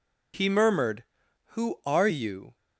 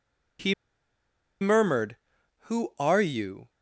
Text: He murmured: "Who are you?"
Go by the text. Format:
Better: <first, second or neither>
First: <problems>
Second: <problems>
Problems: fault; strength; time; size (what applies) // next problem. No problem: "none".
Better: first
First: none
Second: pauses between "He" and "murmured"; noticeable; at 0.5 s; 0.87 s long